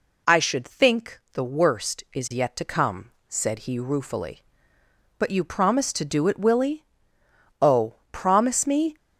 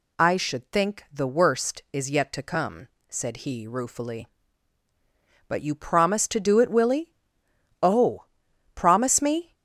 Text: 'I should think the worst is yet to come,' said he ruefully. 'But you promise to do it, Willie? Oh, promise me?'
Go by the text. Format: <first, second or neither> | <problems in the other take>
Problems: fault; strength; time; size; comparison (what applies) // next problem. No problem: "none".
neither | none